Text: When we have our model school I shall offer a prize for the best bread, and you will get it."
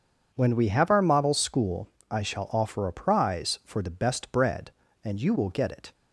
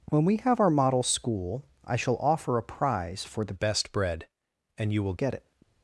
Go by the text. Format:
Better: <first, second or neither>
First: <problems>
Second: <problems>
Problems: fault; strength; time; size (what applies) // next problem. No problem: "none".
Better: first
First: pauses between "school" and "I"; slight; at 1.9 s; 0.20 s long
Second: pauses between "school" and "I"; slight; at 1.6 s; 0.22 s long // changes voice from "best" to "will"; from 3.5 to 5.1 s; 1.6 s long